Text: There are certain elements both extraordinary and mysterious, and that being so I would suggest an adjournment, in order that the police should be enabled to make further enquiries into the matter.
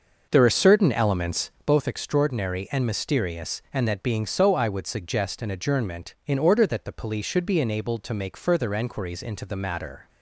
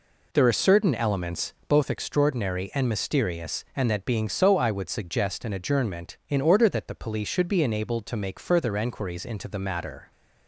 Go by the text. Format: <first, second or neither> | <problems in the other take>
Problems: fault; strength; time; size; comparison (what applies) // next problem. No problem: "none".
second | starts louder than the rest; noticeable; until 1.7 s; 6 dB